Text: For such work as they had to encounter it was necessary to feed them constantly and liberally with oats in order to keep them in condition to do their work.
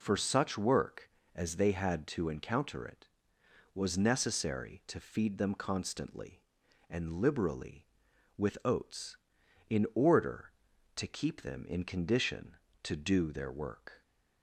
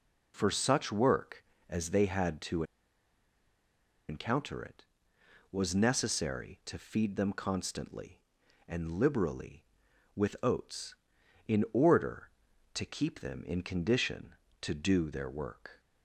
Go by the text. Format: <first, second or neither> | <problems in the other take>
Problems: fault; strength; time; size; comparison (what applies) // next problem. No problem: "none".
first | pauses between "to" and "encounter"; strong; at 2.6 s; 1.4 s long